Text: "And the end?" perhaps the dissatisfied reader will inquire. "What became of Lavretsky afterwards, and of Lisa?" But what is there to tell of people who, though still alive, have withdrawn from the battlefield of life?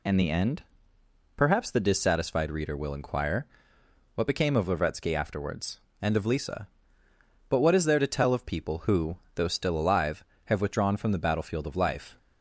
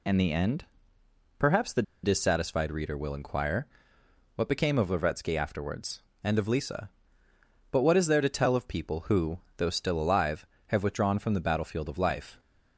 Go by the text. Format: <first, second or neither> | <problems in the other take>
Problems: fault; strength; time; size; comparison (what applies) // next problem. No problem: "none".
first | pauses between "the" and "dissatisfied"; slight; at 1.8 s; 0.20 s long